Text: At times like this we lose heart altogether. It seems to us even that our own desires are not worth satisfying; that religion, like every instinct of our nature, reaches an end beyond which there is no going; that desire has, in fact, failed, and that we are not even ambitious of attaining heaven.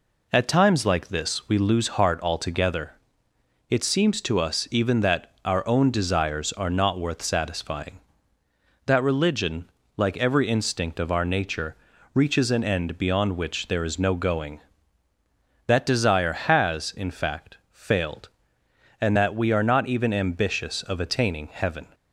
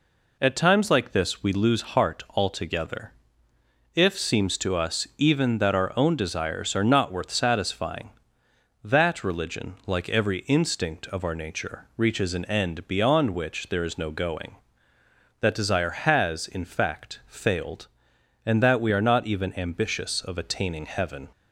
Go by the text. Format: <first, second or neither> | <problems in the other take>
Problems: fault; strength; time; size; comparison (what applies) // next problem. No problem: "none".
first | says "If" for "It"; at 3.9 s